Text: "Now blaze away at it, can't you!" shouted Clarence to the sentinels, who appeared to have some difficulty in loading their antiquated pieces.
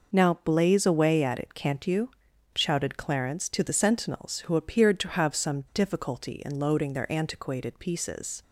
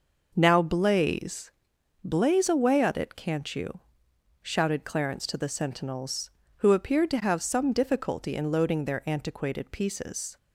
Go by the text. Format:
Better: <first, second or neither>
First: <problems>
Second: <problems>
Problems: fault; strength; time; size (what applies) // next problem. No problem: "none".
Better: first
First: none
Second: says "blaze" twice; at 2.0 s